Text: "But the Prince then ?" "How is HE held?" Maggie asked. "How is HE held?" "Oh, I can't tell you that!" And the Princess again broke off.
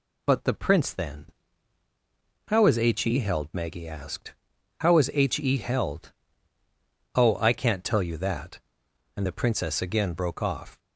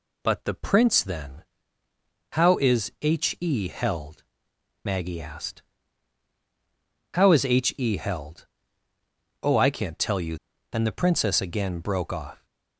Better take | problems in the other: first | skips "that"; at 10.5 s

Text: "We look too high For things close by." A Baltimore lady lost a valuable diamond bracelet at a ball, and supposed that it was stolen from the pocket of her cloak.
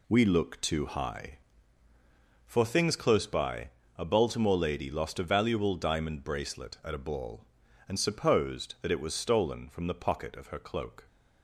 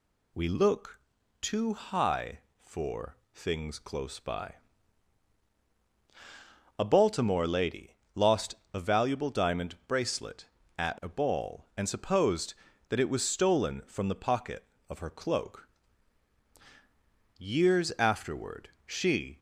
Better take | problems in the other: first | pauses between "look" and "too"; at 0.9 s; 0.42 s long // pauses between "For" and "things"; slight; at 3.1 s; 0.16 s long // pauses between "lady" and "lost"; slight; at 7.9 s; 0.22 s long // pauses between "lost" and "a"; slight; at 8.5 s; 0.16 s long // goes on to say "Years afterward she"; strong; from 17.3 s on; 2.0 s long

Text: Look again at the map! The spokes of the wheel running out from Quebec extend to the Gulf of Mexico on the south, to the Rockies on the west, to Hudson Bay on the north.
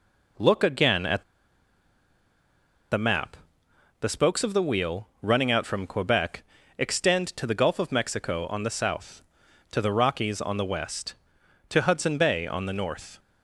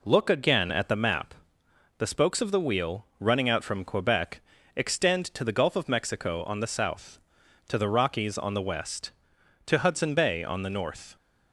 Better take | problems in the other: second | pauses between "at" and "the"; strong; at 1.2 s; 1.6 s long // pauses between "Quebec" and "extend"; slight; at 6.4 s; 0.34 s long; slight in the second

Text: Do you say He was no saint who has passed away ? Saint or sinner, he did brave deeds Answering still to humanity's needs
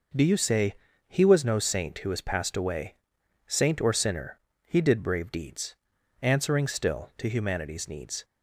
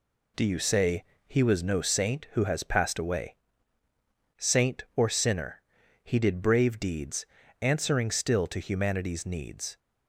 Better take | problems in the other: neither | pauses between "say" and "He"; slight; the same in both // pauses between "deeds" and "Answering"; the same in both

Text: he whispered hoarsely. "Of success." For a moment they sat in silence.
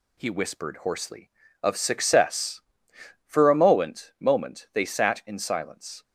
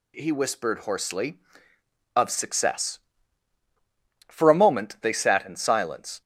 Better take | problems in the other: second | says "moment" twice; at 4.1 s

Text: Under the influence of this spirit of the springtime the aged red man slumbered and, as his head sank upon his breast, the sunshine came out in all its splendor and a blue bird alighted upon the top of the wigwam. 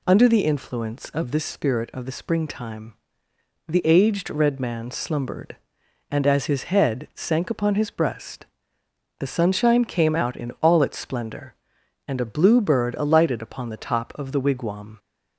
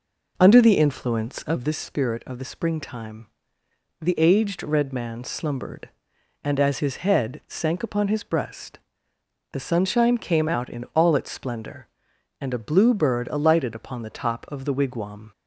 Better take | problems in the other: first | starts louder than the rest; noticeable; until 1.7 s; 4.5 dB // pauses between "springtime" and "the"; noticeable; at 3.2 s; 0.74 s long; noticeable in the first

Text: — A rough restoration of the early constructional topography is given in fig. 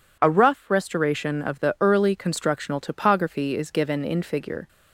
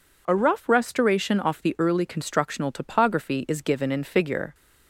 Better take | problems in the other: first | says "off" for "of"; at 1.4 s

